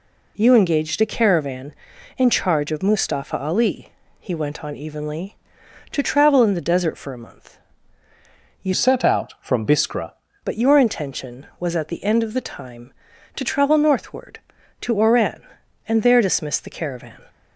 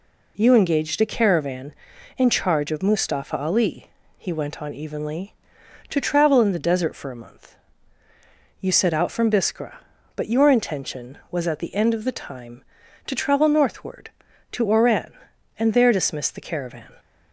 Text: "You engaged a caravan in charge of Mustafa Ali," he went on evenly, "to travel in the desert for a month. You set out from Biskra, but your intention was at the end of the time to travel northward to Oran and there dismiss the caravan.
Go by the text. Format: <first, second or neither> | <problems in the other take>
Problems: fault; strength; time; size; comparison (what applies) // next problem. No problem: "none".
second | changes voice from "set" to "Biskra"; from 8.7 to 10.1 s; 1.4 s long